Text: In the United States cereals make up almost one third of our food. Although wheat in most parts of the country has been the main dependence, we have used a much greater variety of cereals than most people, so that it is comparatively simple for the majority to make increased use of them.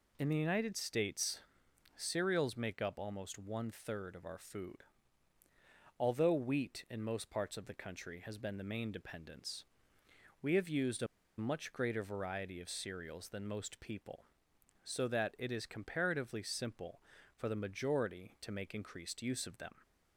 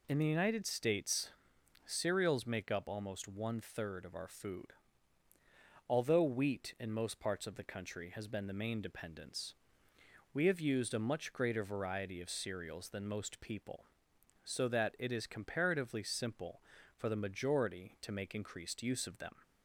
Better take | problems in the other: second | pauses between "States" and "cereals"; noticeable; at 1.4 s; 0.56 s long; noticeable in the second // pauses between "a" and "much"; slight; at 11.0 s; 0.33 s long

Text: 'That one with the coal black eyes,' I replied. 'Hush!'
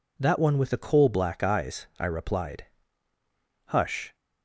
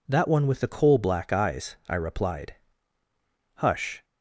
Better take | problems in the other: neither | none

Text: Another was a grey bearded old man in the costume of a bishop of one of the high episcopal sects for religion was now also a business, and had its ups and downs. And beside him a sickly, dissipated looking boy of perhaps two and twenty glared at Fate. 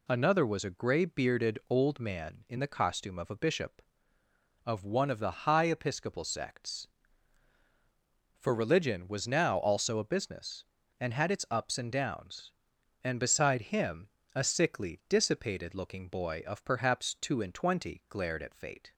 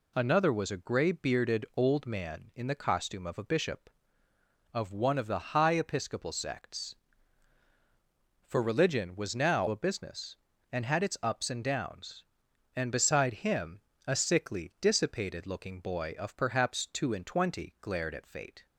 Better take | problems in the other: first | skips "also"; at 9.6 s // pauses between "him" and "a"; slight; at 13.7 s; 0.28 s long; slight in the first

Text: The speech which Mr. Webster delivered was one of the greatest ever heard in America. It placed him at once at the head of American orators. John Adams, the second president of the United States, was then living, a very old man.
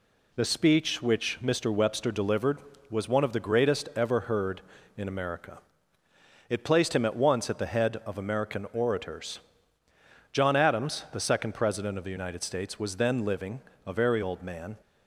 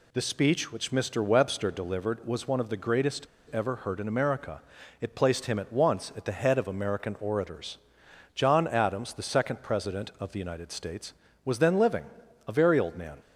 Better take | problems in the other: first | pauses between "greatest" and "ever"; slight; at 3.2 s; 0.25 s long

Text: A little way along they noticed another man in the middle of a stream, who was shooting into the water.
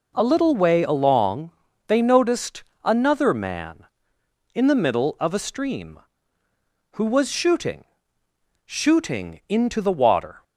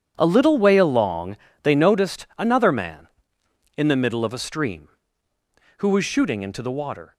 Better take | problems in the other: second | pauses between "along" and "they"; at 1.4 s; 0.38 s long; slight in the second // pauses between "noticed" and "another"; slight; at 2.6 s; 0.22 s long // says "shooting" twice; at 8.6 s

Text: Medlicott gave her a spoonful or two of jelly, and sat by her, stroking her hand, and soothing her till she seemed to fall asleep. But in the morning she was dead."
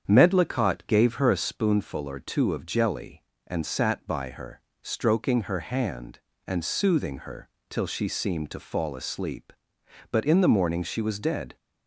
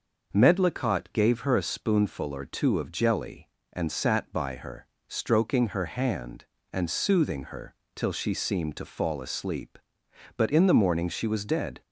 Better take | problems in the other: second | starts louder than the rest; strong; until 1.6 s; 8 dB // pauses between "her" and "till"; slight; at 7.4 s; 0.20 s long; slight in the second

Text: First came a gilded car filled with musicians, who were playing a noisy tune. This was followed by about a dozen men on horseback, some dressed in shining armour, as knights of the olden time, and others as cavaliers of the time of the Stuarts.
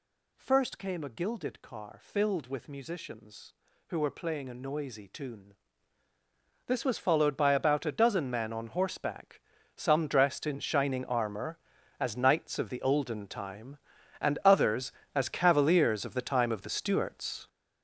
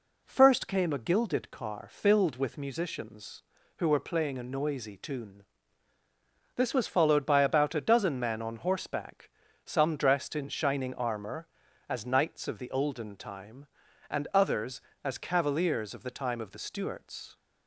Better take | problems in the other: second | gets louder; strong; throughout; 9.5 dB

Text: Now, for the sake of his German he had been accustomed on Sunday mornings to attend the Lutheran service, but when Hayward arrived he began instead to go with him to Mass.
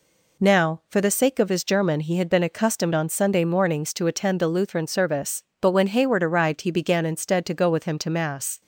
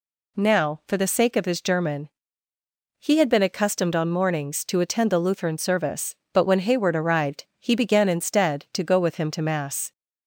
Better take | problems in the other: first | pauses between "German" and "he"; noticeable; at 2.0 s; 0.96 s long // skips "Sunday"; at 4.1 s

